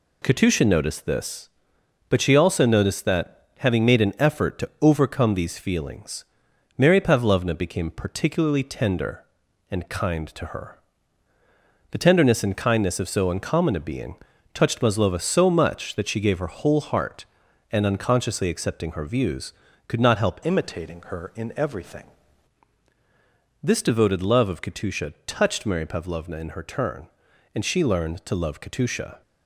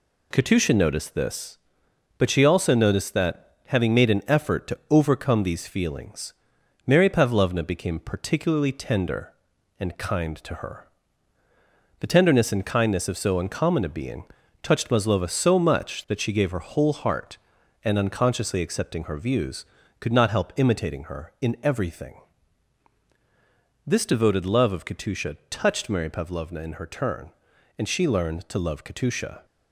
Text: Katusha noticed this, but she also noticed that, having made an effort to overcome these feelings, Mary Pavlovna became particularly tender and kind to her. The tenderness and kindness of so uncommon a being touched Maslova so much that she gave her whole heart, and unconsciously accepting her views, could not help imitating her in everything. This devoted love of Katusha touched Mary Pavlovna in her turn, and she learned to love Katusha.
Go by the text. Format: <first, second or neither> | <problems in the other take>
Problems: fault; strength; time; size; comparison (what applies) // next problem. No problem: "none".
second | pauses between "being" and "touched"; at 14.1 s; 0.38 s long; also in the second // changes voice from "imitating" to "everything"; from 20.4 to 22.0 s; 1.6 s long